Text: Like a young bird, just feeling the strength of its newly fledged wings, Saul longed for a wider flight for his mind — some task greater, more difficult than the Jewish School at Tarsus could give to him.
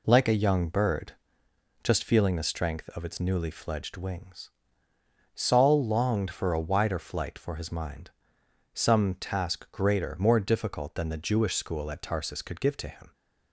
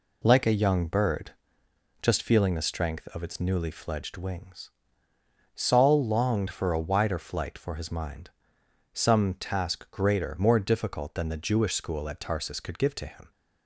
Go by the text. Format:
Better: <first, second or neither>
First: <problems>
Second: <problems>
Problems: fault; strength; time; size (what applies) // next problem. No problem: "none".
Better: neither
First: none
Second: none